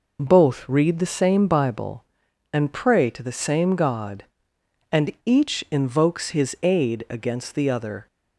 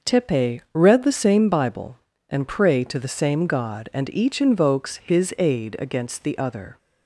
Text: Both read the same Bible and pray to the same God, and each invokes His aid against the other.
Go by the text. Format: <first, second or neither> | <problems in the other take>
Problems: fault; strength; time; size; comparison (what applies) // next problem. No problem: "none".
first | says "Tepe" for "Both"; at 0.0 s